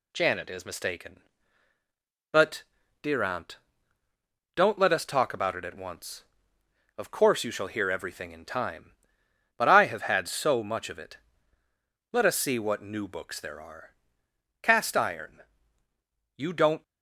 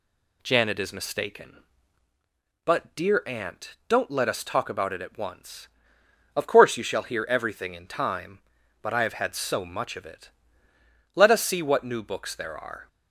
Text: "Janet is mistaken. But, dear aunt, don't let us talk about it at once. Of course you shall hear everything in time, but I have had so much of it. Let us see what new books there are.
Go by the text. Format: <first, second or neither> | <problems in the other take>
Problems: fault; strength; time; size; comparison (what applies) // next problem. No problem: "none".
second | goes on to say "Cast Iron You don't"; strong; from 14.6 s on; 2.2 s long